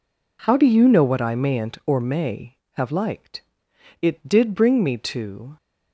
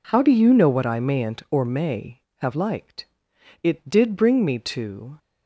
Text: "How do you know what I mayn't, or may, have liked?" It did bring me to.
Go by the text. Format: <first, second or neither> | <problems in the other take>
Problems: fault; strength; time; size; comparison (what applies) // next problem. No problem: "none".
neither | none